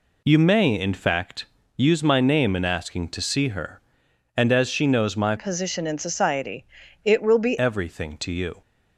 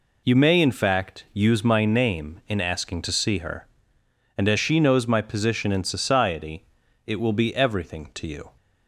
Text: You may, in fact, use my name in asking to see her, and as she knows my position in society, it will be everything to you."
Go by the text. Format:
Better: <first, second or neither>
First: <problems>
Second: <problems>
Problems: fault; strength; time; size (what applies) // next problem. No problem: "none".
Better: second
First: changes voice from "position" to "be"; from 5.3 to 7.5 s; 2.2 s long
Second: none